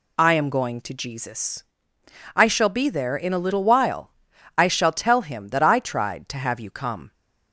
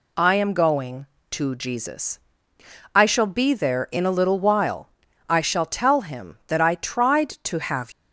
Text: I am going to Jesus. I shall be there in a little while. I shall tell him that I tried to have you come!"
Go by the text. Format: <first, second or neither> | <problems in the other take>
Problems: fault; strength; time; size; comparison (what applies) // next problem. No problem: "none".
first | stops before "you come"; at 7.9 s